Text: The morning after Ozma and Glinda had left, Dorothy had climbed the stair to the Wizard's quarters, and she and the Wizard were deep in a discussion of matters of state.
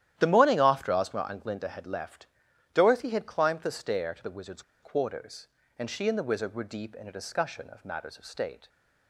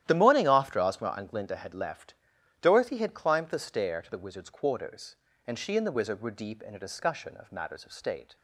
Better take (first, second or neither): second